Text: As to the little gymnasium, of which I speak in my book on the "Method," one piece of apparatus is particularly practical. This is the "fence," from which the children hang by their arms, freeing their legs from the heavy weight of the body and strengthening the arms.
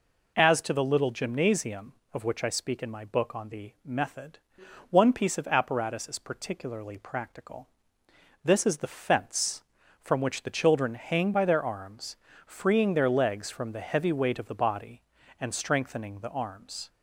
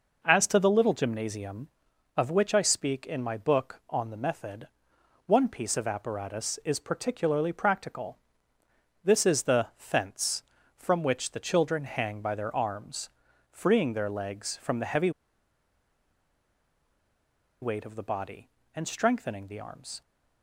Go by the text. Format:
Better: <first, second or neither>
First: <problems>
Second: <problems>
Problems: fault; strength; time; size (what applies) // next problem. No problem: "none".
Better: first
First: none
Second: pauses between "heavy" and "weight"; strong; at 15.0 s; 2.5 s long